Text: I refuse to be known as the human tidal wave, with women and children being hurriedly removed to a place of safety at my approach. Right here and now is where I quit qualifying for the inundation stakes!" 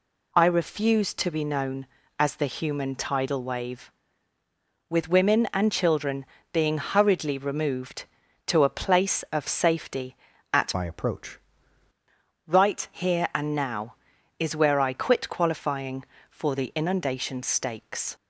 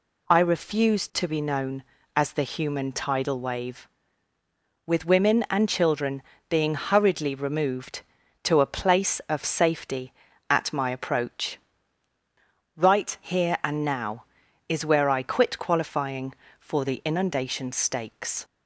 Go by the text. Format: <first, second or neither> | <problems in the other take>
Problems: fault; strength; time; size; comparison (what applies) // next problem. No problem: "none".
second | pauses between "children" and "being"; slight; at 6.2 s; 0.30 s long; slight in the second // changes voice from "my" to "approach"; from 10.7 to 11.3 s; 0.6 s long